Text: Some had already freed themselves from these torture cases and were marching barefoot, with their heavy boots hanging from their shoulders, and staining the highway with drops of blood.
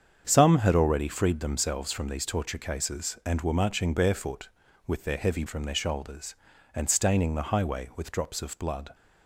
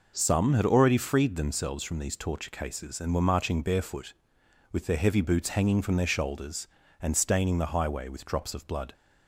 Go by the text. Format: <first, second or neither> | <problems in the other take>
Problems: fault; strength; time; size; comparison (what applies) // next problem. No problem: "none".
second | starts louder than the rest; strong; until 1.2 s; 7.5 dB // skips "boots hanging"; at 5.4 s